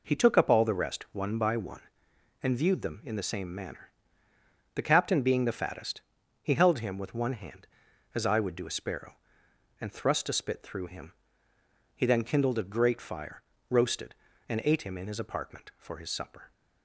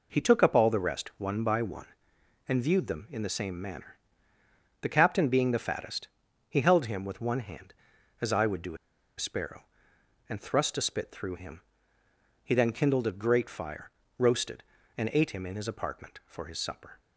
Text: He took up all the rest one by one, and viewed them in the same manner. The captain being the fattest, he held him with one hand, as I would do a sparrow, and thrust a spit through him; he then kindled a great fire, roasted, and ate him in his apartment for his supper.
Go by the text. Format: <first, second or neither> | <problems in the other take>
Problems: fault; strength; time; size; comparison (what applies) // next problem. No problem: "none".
first | pauses between "a" and "sparrow"; at 8.7 s; 0.42 s long